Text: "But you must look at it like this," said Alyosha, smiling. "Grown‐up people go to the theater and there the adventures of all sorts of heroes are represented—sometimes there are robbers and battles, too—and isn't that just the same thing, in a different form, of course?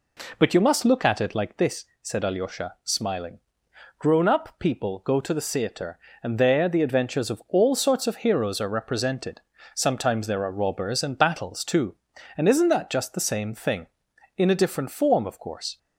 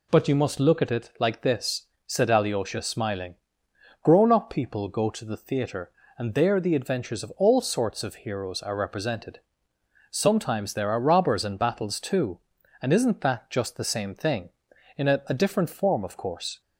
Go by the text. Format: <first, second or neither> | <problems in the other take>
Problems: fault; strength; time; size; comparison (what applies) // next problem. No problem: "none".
first | says "a" twice; at 15.2 s